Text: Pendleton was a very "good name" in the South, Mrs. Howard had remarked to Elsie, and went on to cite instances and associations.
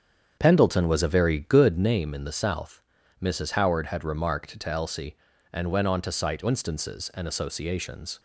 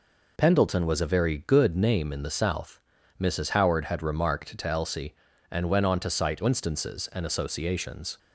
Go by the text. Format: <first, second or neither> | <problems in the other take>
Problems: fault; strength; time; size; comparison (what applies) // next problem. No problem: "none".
second | starts louder than the rest; strong; until 2.0 s; 8 dB